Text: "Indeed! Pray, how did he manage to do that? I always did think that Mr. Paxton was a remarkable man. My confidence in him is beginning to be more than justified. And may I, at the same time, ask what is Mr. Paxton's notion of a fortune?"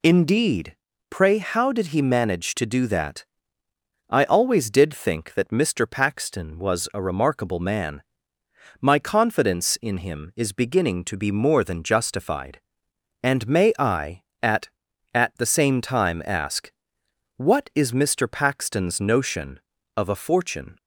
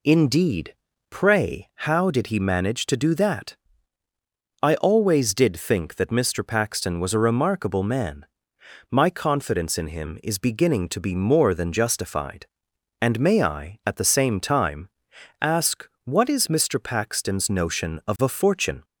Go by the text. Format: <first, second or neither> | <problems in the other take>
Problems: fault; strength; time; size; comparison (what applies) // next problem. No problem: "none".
second | says "at" twice; at 15.1 s // pauses between "ask" and "what"; noticeable; at 16.7 s; 0.66 s long; slight in the second